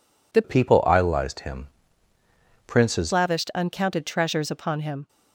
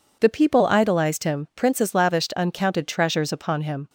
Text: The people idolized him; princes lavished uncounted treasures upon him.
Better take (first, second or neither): second